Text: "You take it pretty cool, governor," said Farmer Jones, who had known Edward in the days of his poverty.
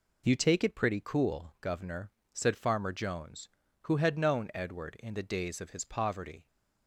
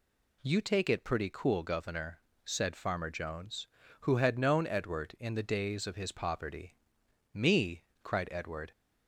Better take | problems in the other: first | goes on to say "Me cried Edward"; from 7.3 s on; 1.3 s long

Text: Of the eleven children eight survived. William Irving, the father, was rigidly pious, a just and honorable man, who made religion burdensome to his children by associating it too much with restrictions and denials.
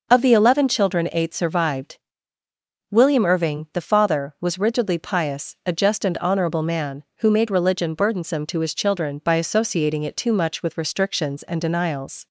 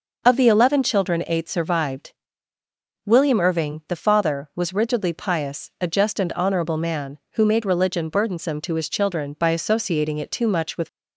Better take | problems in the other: first | stops before "restrictions and denials"; at 10.8 s

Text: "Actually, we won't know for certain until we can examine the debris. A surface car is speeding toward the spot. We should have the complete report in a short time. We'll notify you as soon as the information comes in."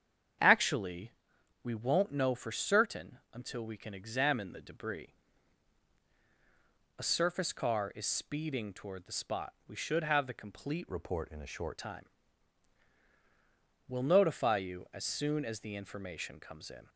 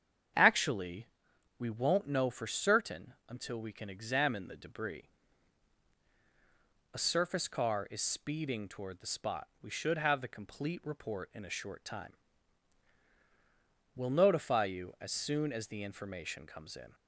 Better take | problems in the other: second | starts louder than the rest; strong; until 1.9 s; 8 dB; strong in the second // pauses between "certain" and "until"; slight; at 3.1 s; 0.16 s long; slight in the second // changes voice from "report" to "short"; from 10.9 to 11.7 s; 0.8 s long

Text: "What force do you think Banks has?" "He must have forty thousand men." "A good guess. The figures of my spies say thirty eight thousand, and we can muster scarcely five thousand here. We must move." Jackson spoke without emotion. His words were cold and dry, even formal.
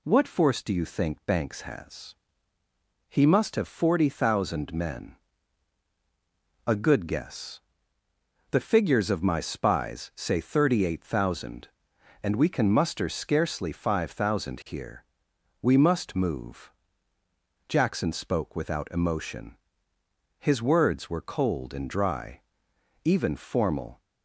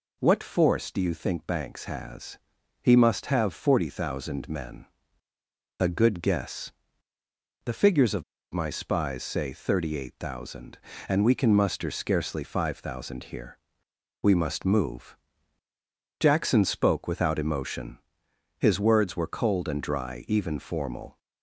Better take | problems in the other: first | pauses between "of" and "my"; slight; at 8.2 s; 0.30 s long

